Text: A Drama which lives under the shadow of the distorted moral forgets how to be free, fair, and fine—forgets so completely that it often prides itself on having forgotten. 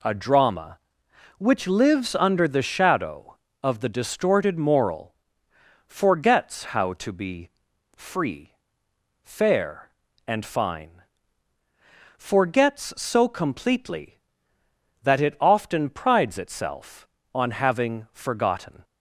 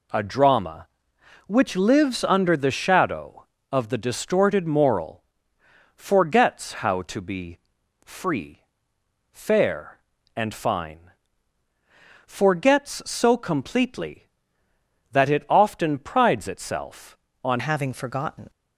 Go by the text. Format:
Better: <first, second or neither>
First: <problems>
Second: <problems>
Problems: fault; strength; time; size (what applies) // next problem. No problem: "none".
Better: first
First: pauses between "moral" and "forgets"; noticeable; at 5.1 s; 0.72 s long // pauses between "be" and "free"; noticeable; at 7.4 s; 0.46 s long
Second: pauses between "moral" and "forgets"; noticeable; at 5.2 s; 0.72 s long // pauses between "be" and "free"; noticeable; at 7.5 s; 0.46 s long // changes voice at "having"; from 17.5 s on; 0.9 s long